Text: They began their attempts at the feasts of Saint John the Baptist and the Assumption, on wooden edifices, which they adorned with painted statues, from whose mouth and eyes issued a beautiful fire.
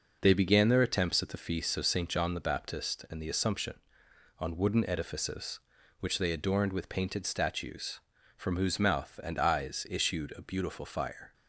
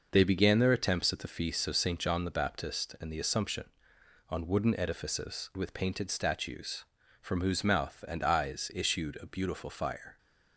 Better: first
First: none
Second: skips "which they adorned"; at 5.5 s

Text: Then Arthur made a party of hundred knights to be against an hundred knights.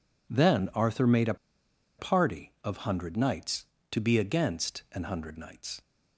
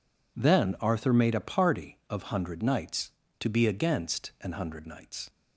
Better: second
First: pauses between "a" and "party"; noticeable; at 1.3 s; 0.62 s long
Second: none

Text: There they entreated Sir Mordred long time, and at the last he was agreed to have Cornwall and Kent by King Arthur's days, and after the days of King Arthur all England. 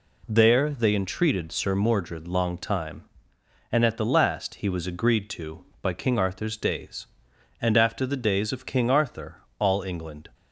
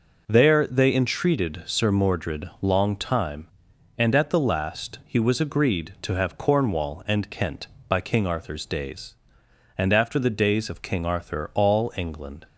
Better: second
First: skips "have Cornwall and Kent"; at 5.7 s // pauses between "Arthur" and "all"; slight; at 9.4 s; 0.16 s long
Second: none

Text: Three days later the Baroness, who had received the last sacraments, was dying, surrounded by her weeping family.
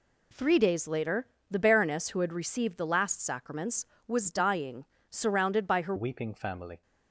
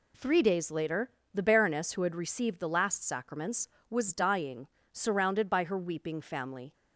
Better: second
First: pauses between "later" and "the"; slight; at 1.2 s; 0.24 s long // changes voice at "weeping"; from 5.9 s on; 0.9 s long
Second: pauses between "later" and "the"; slight; at 1.0 s; 0.24 s long

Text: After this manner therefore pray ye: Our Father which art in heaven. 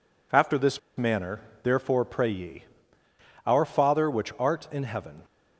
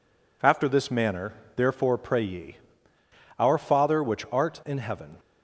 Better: second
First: pauses between "this" and "manner"; slight; at 0.7 s; 0.18 s long // pauses between "manner" and "therefore"; slight; at 1.4 s; 0.22 s long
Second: pauses between "manner" and "therefore"; slight; at 1.3 s; 0.22 s long

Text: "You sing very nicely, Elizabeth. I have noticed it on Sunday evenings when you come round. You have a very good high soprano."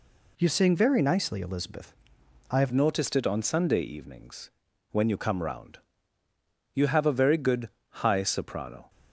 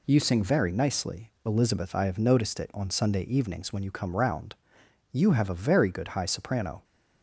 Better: second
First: changes voice at "noticed"; from 2.7 s on; 6.1 s long // pauses between "evenings" and "when"; at 4.4 s; 0.42 s long // pauses between "good" and "high"; slight; at 7.6 s; 0.32 s long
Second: none

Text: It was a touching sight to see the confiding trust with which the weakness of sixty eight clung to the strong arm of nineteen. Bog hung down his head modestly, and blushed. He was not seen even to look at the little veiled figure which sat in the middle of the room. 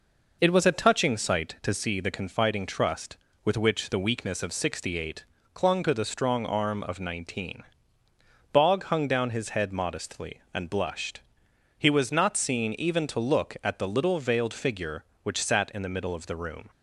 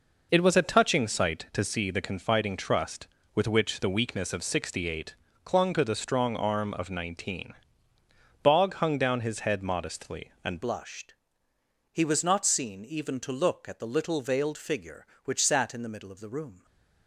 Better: first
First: pauses between "eight" and "clung"; slight; at 5.2 s; 0.28 s long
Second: pauses between "eight" and "clung"; slight; at 5.1 s; 0.28 s long // changes voice at "blushed"; from 10.6 s on; 6.0 s long

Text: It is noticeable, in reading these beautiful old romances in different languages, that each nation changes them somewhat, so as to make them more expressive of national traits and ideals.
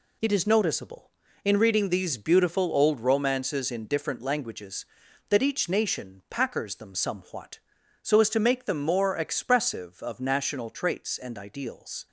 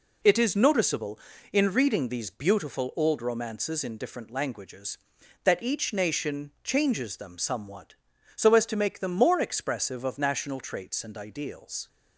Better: second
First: says "packers" for "changes"; at 6.2 s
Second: none

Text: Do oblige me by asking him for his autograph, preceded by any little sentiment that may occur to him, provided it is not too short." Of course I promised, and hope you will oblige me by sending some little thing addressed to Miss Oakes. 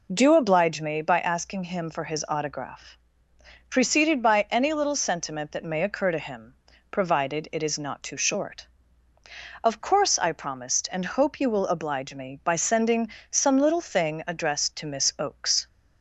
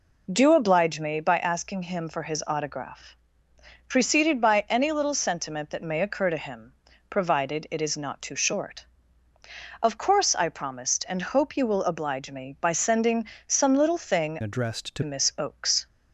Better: first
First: pauses between "sending" and "some"; slight; at 13.0 s; 0.20 s long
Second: pauses between "sending" and "some"; slight; at 13.2 s; 0.20 s long // changes voice from "addressed" to "to"; from 14.4 to 15.0 s; 0.6 s long

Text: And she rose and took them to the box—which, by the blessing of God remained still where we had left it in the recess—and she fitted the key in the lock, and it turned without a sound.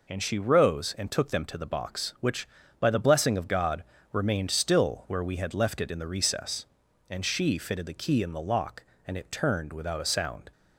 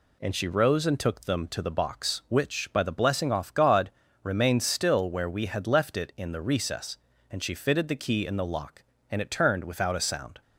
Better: first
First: pauses between "God" and "remained"; slight; at 3.8 s; 0.28 s long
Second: says "off" for "of"; at 3.3 s // pauses between "God" and "remained"; slight; at 3.9 s; 0.32 s long

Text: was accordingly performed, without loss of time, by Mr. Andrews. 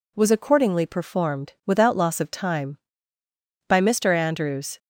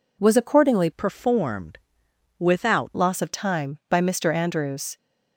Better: first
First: none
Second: changes voice from "performed" to "without"; from 0.9 to 2.9 s; 2.0 s long

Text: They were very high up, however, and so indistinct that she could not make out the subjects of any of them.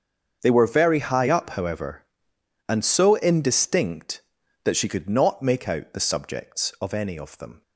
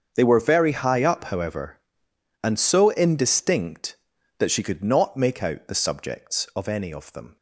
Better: neither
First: starts louder than the rest; until 1.4 s; 7 dB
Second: starts louder than the rest; until 1.1 s; 7 dB

